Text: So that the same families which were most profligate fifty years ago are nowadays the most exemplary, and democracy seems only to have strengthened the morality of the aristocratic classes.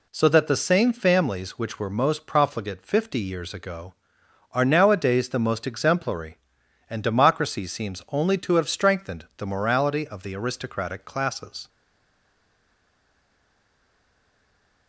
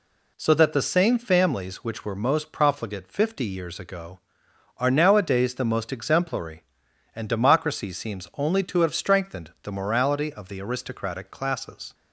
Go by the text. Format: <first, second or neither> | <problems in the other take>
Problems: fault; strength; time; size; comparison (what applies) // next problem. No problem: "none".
second | stays silent after the last word; strong; from 11.6 s on; 3.2 s long